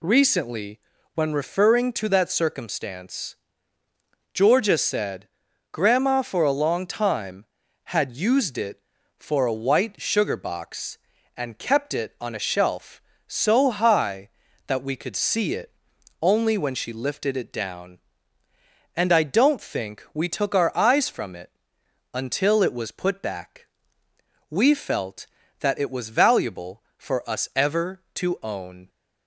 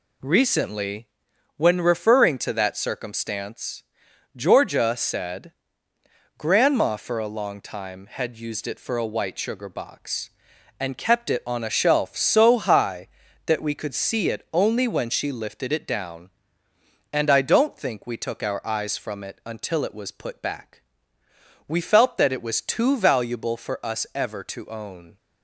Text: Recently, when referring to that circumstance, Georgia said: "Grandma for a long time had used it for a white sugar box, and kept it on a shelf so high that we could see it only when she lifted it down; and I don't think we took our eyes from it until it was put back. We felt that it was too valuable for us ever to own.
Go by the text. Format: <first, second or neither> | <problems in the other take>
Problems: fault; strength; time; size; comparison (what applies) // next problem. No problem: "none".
second | pauses between "it" and "only"; noticeable; at 15.7 s; 0.50 s long // pauses between "it" and "until"; noticeable; at 21.5 s; 0.62 s long // skips "too"; at 26.1 s